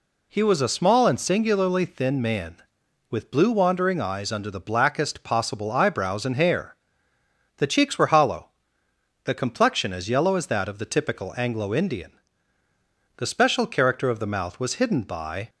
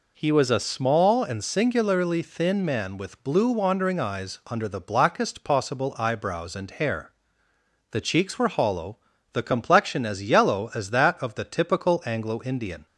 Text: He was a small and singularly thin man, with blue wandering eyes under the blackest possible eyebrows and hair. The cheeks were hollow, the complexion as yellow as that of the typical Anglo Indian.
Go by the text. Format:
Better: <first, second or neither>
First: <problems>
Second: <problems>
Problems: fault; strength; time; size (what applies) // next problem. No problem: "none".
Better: second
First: goes on to say "The special character of the mouth was hidden by"; strong; from 13.1 s on; 2.3 s long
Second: none